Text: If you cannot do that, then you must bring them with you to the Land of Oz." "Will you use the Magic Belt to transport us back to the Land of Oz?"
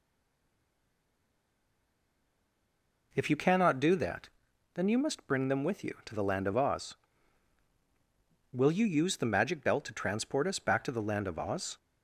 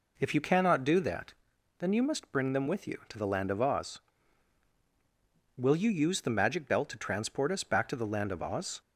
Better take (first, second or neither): second